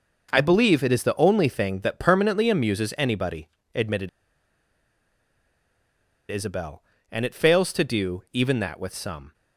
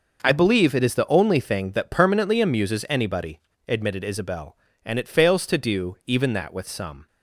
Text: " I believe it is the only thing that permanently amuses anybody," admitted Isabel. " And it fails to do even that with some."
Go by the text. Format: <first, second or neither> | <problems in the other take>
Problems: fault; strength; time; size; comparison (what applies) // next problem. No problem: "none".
second | pauses between "admitted" and "Isabel"; strong; at 4.0 s; 2.2 s long